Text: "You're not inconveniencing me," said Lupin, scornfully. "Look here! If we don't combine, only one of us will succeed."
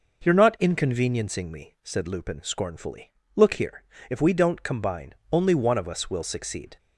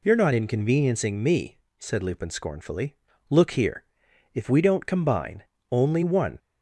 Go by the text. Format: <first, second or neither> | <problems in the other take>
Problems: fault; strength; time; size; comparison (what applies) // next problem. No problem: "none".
first | stops before "of us will succeed"; at 6.3 s